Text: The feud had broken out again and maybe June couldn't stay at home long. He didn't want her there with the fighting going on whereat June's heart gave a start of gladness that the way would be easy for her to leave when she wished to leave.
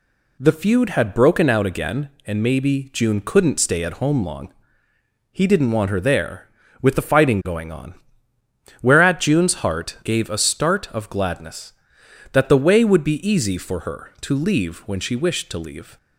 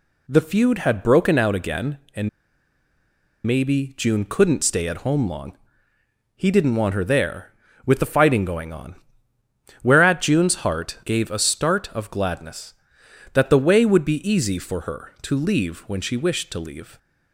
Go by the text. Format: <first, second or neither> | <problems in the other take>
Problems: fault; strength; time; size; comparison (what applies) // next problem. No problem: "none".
first | pauses between "and" and "maybe"; at 2.2 s; 1.1 s long // pauses between "on" and "whereat"; noticeable; at 8.9 s; 0.88 s long; noticeable in the first